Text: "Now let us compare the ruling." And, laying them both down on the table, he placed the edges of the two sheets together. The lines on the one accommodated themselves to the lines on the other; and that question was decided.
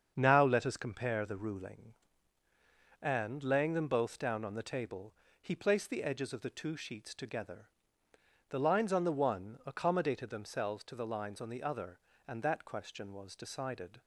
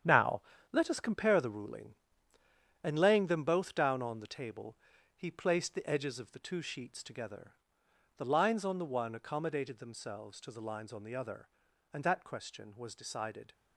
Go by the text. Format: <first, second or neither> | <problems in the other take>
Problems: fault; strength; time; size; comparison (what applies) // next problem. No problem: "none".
first | gets quieter; strong; throughout; 10 dB // starts louder than the rest; strong; until 1.3 s; 9 dB; strong in the first // pauses between "Now" and "let"; slight; at 0.4 s; 0.32 s long